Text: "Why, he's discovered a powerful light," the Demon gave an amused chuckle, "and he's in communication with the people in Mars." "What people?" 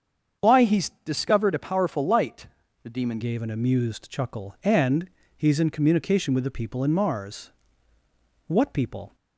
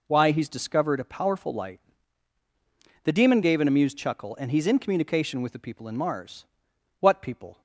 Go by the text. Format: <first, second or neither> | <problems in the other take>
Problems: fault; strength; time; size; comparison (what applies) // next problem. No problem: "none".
second | starts louder than the rest; strong; until 1.5 s; 7.5 dB // changes voice at "gave"; from 3.2 s on; 5.9 s long // pauses between "and" and "he's"; slight; at 5.0 s; 0.30 s long